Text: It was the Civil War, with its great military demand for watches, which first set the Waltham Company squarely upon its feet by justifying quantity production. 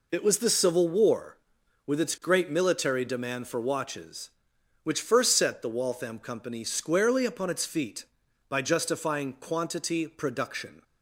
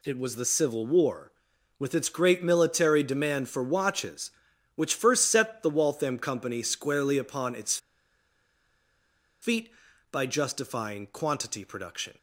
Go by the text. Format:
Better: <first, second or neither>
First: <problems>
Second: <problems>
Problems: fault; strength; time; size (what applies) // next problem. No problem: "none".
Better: first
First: none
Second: pauses between "its" and "feet"; strong; at 7.7 s; 1.6 s long